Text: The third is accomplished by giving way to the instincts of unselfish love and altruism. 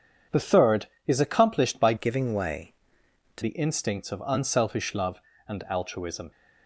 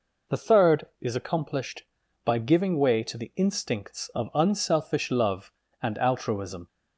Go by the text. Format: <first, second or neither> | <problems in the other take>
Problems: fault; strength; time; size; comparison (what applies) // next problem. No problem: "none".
second | changes voice from "giving" to "to"; from 1.9 to 3.4 s; 1.5 s long